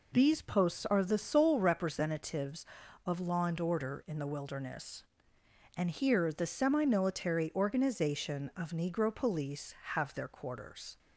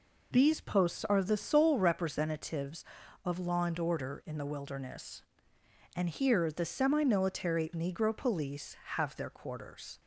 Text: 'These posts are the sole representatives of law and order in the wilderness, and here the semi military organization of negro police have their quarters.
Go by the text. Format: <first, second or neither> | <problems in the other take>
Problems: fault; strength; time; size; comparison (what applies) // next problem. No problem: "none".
first | skips "organization of"; at 7.7 s